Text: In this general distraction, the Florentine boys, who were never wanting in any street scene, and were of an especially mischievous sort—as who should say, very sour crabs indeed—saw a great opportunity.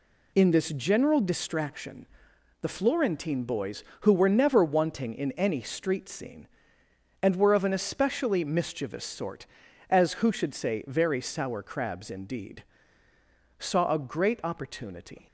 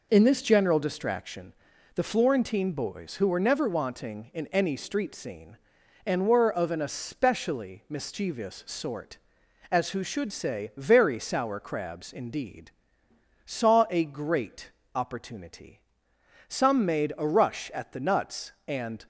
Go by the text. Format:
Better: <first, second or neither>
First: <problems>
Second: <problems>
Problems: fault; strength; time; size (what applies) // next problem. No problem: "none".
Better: first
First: none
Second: pauses between "great" and "opportunity"; slight; at 14.7 s; 0.24 s long // goes on to say "Some made a rush at the nuts and"; strong; from 16.4 s on; 2.5 s long